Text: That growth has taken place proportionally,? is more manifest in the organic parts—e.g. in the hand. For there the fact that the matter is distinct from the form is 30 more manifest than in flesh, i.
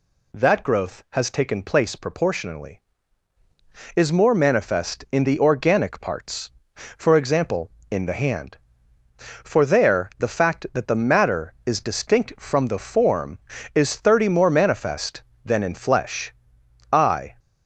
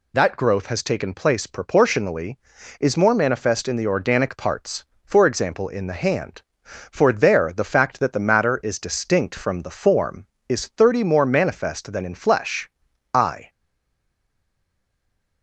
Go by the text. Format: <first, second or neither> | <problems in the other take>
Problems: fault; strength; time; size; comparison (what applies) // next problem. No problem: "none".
first | stays silent after the last word; noticeable; from 13.4 s on; 2.0 s long